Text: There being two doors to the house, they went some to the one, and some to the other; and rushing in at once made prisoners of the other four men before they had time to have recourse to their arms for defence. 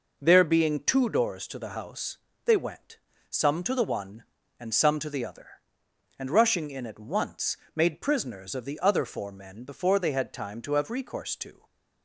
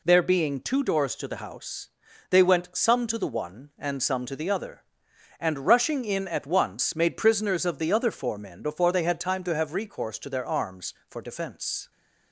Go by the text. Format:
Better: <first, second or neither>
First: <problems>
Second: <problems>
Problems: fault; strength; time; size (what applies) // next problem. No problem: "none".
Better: second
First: pauses between "went" and "some"; slight; at 2.9 s; 0.32 s long // pauses between "once" and "made"; slight; at 7.5 s; 0.20 s long // stops before "their arms for defence"; at 11.6 s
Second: none